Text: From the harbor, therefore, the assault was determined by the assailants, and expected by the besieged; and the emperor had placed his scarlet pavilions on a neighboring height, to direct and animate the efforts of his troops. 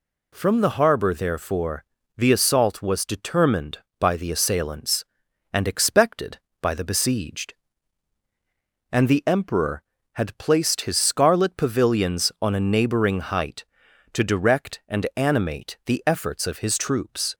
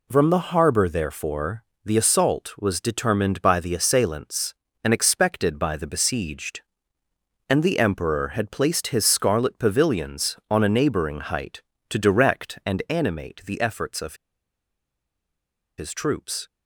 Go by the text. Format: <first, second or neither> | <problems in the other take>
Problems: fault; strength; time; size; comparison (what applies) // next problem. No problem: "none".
first | pauses between "of" and "his"; strong; at 14.1 s; 1.6 s long